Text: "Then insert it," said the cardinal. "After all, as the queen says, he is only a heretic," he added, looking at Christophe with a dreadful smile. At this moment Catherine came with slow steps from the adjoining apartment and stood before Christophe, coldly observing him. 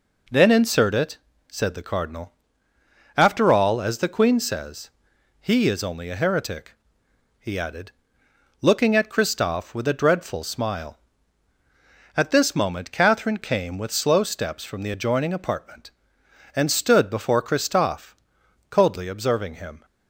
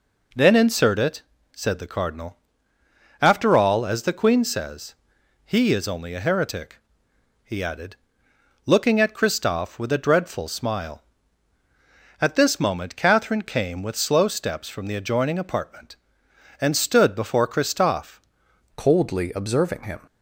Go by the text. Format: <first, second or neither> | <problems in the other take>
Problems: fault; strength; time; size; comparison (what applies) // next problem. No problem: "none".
first | changes voice at "coldly"; from 18.7 s on; 1.2 s long